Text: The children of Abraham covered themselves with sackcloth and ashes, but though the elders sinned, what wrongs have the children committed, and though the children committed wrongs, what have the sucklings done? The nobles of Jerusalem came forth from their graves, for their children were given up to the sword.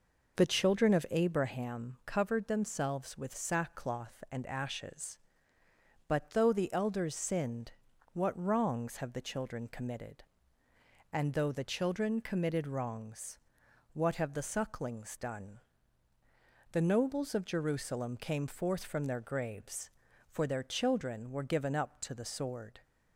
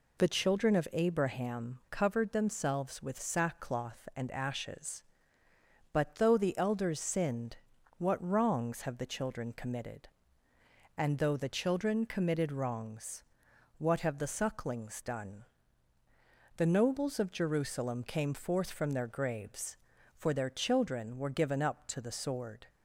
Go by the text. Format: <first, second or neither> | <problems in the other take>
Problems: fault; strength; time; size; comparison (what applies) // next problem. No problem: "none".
second | starts louder than the rest; noticeable; until 1.5 s; 5.5 dB